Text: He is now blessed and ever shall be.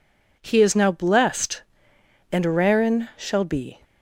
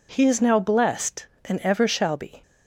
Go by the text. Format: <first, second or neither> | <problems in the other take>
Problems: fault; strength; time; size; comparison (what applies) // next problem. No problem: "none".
second | says "rarin" for "ever"; at 2.4 s